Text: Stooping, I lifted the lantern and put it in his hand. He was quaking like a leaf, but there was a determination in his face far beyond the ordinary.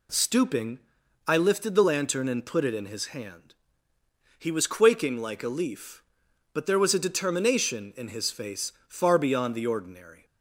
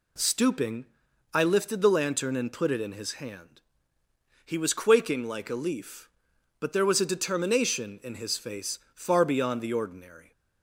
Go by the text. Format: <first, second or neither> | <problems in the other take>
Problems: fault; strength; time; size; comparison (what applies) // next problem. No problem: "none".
neither | pauses between "face" and "far"; slight; the same in both